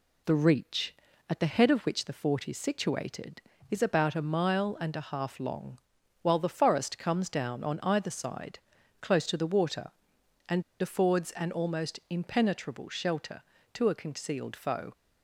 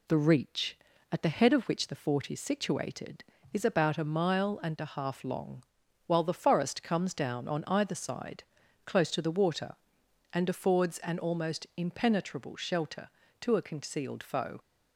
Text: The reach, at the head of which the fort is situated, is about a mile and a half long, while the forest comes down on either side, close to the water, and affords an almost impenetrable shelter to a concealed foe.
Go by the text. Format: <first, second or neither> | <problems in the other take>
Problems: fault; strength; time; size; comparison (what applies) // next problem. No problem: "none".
second | pauses between "and" and "affords"; slight; at 10.6 s; 0.17 s long